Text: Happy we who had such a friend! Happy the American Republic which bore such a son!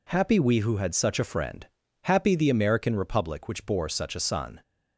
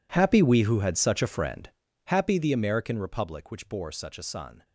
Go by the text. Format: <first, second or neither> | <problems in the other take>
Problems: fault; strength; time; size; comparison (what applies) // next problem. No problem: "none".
first | gets quieter; strong; throughout; 18.5 dB